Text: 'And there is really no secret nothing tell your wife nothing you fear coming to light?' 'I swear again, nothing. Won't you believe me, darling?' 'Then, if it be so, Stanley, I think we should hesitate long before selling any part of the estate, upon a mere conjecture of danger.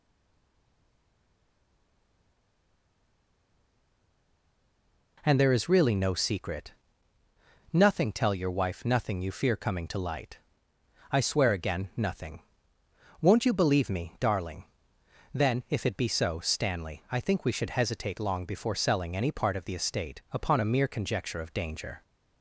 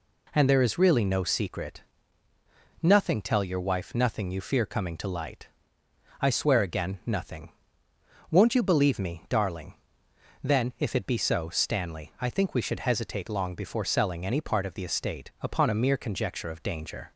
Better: second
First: stays silent before the first word; strong; until 5.1 s; 5.1 s long // pauses between "secret" and "nothing"; noticeable; at 6.7 s; 0.98 s long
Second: pauses between "secret" and "nothing"; noticeable; at 1.8 s; 0.98 s long

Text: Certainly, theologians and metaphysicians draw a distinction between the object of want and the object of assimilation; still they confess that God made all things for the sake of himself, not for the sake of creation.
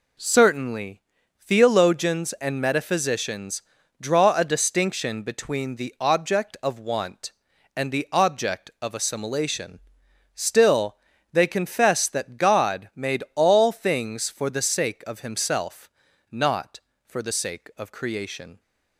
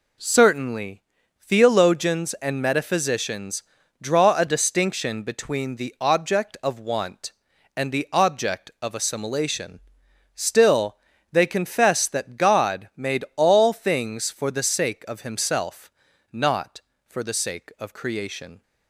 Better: neither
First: pauses between "metaphysicians" and "draw"; at 3.6 s; 0.38 s long // pauses between "still" and "they"; slight; at 10.9 s; 0.36 s long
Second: pauses between "metaphysicians" and "draw"; at 3.6 s; 0.38 s long // pauses between "still" and "they"; slight; at 10.9 s; 0.35 s long

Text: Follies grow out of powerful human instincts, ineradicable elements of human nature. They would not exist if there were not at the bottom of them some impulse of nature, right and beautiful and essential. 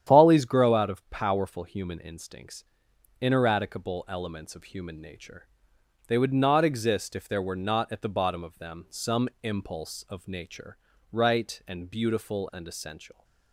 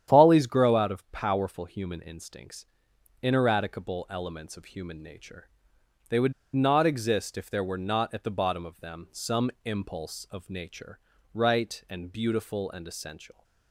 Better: first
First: starts louder than the rest; strong; until 1.1 s; 9.5 dB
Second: starts louder than the rest; strong; until 1.1 s; 9.5 dB // pauses between "would" and "not"; slight; at 6.3 s; 0.20 s long

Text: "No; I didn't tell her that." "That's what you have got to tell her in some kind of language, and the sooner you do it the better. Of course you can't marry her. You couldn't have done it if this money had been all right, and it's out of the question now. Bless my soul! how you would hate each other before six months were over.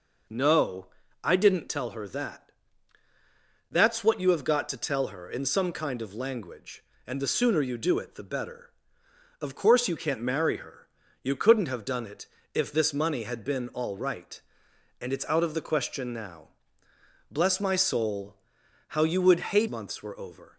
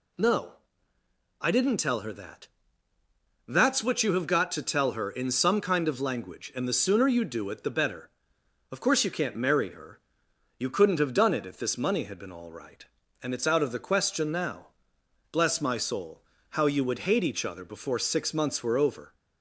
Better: second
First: pauses between "it" and "if"; slight; at 12.2 s; 0.30 s long // skips "each other before six"; at 19.6 s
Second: none

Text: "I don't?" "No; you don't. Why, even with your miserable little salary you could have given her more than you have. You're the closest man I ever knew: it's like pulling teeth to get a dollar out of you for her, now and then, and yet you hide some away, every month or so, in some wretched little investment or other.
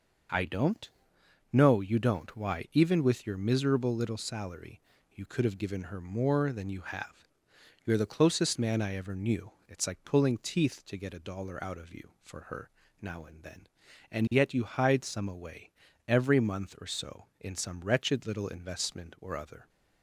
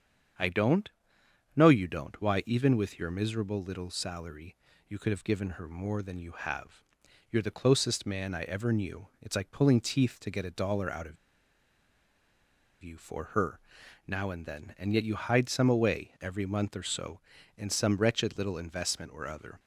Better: first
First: pauses between "salary" and "you"; slight; at 4.8 s; 0.30 s long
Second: starts louder than the rest; strong; until 2.0 s; 7.5 dB // pauses between "salary" and "you"; slight; at 4.5 s; 0.32 s long // pauses between "of" and "you"; strong; at 11.1 s; 1.6 s long

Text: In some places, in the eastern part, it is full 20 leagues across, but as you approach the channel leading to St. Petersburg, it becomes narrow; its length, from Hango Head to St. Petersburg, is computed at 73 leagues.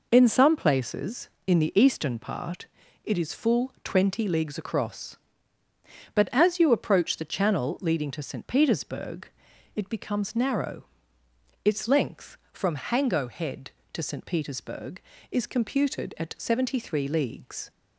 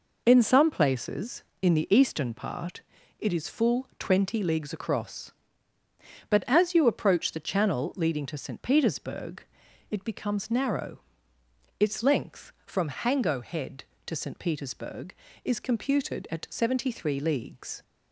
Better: neither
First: none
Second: none

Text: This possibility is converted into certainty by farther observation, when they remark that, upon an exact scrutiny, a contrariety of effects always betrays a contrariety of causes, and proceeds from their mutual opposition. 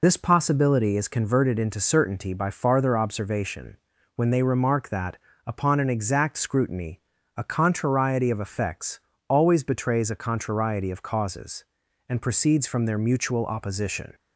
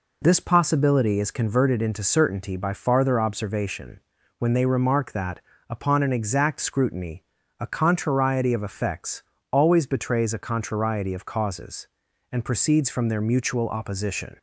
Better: second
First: loses the start of "This"; at 0.0 s; 40 ms // pauses between "effects" and "always"; slight; at 8.9 s; 0.28 s long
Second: pauses between "effects" and "always"; slight; at 9.2 s; 0.28 s long

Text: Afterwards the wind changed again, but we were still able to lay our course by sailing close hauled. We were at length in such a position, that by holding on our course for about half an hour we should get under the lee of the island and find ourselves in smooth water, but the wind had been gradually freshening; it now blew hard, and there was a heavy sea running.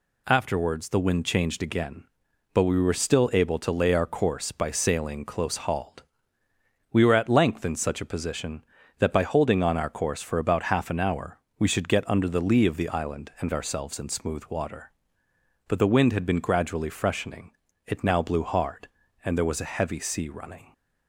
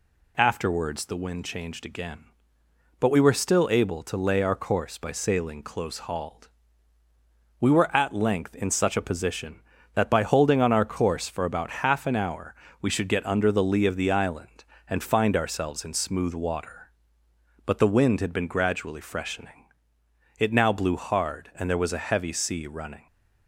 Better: second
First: pauses between "hour" and "we"; slight; at 11.3 s; 0.20 s long // skips "find"; at 13.5 s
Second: pauses between "hour" and "we"; slight; at 12.5 s; 0.26 s long

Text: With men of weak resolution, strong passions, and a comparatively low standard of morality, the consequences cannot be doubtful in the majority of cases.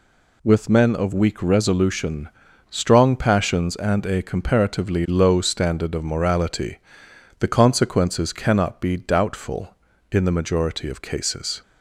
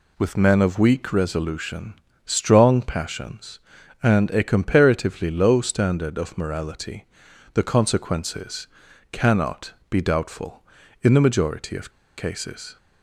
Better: first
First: none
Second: pauses between "consequences" and "cannot"; at 8.6 s; 0.44 s long // pauses between "cannot" and "be"; slight; at 9.7 s; 0.16 s long // pauses between "of" and "cases"; slight; at 11.9 s; 0.26 s long

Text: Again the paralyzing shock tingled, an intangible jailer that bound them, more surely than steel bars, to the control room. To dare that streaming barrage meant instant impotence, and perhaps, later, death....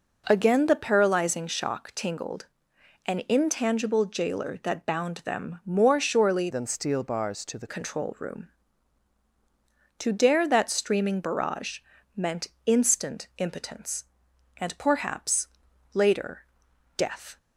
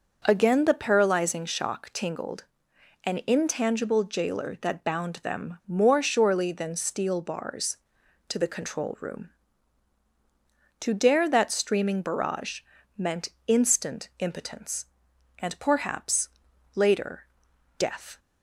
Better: second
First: changes voice from "than" to "the"; from 6.4 to 7.6 s; 1.2 s long // pauses between "barrage" and "meant"; slight; at 11.7 s; 0.36 s long // pauses between "meant" and "instant"; slight; at 12.4 s; 0.18 s long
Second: pauses between "barrage" and "meant"; slight; at 12.6 s; 0.36 s long // pauses between "meant" and "instant"; slight; at 13.2 s; 0.18 s long

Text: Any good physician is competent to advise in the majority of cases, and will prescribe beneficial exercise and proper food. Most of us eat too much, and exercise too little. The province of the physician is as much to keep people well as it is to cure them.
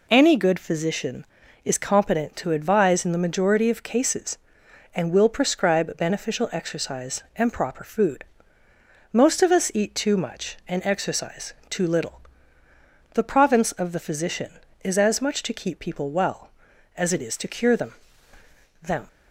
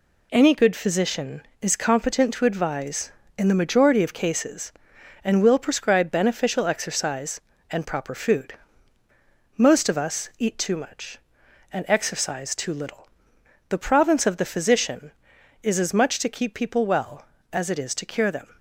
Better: second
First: pauses between "exercise" and "too"; slight; at 11.5 s; 0.16 s long // says "them" twice; at 18.8 s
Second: none

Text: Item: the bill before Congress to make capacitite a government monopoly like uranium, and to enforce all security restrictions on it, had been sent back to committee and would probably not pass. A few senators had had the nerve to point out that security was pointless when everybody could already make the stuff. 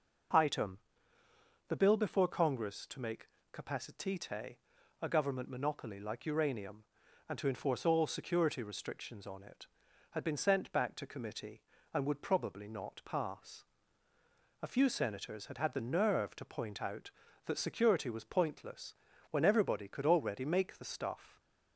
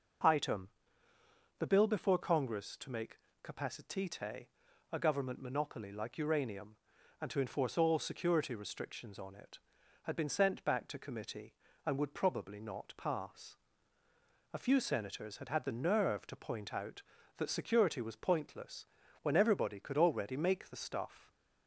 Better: neither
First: pauses between "make" and "capacitite"; slight; at 3.2 s; 0.24 s long // pauses between "capacitite" and "a"; noticeable; at 4.5 s; 0.46 s long // pauses between "pointless" and "when"; at 18.9 s; 0.38 s long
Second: pauses between "make" and "capacitite"; slight; at 3.1 s; 0.24 s long // pauses between "capacitite" and "a"; noticeable; at 4.4 s; 0.46 s long // pauses between "pointless" and "when"; at 18.8 s; 0.38 s long

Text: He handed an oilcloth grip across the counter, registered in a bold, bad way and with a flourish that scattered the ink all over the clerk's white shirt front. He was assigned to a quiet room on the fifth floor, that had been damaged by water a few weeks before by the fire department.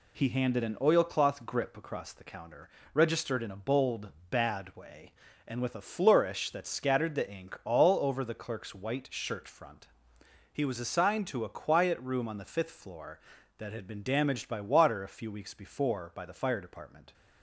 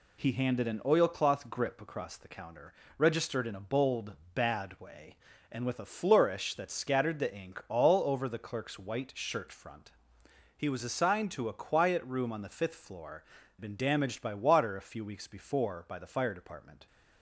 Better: first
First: none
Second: skips "that had"; at 13.4 s

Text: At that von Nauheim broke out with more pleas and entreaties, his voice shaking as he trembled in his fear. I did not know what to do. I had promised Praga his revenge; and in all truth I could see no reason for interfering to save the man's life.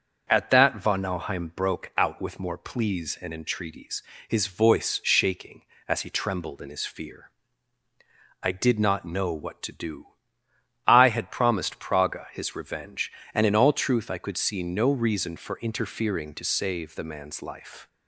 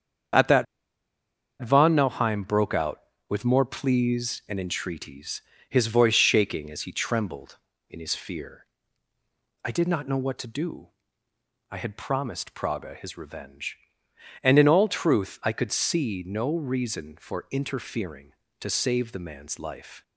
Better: first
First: none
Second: starts louder than the rest; strong; until 2.3 s; 8 dB // pauses between "that" and "von"; noticeable; at 0.6 s; 0.97 s long

